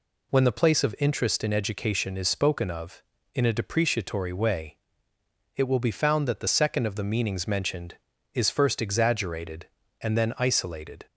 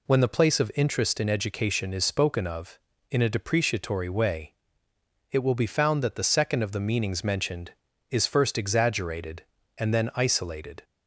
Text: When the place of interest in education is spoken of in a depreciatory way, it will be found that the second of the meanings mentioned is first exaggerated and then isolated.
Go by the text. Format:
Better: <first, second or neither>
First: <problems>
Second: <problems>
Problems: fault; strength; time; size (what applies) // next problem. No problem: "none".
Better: neither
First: none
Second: none